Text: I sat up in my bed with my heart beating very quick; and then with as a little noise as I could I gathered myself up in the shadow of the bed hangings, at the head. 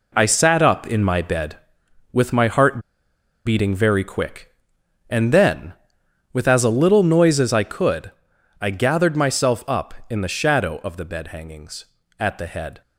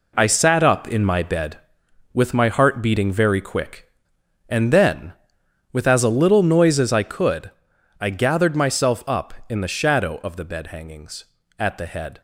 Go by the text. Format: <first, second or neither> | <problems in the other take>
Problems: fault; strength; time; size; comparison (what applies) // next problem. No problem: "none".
second | pauses between "heart" and "beating"; noticeable; at 2.7 s; 0.66 s long // pauses between "could" and "I"; noticeable; at 8.1 s; 0.50 s long; noticeable in the second